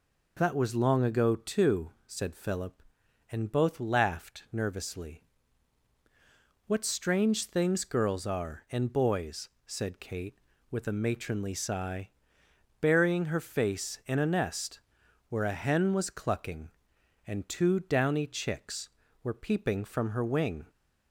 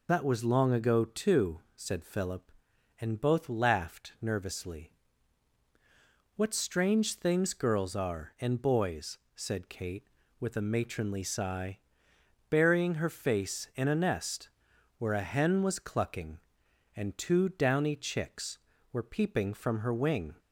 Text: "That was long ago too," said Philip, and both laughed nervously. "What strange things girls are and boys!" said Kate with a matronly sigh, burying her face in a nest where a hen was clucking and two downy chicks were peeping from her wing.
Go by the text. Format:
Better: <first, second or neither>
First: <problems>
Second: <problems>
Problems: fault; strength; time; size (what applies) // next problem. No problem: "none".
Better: first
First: pauses between "nest" and "where"; noticeable; at 14.7 s; 0.50 s long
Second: loses the start of "That"; at 0.0 s; 35 ms // pauses between "nest" and "where"; noticeable; at 14.4 s; 0.50 s long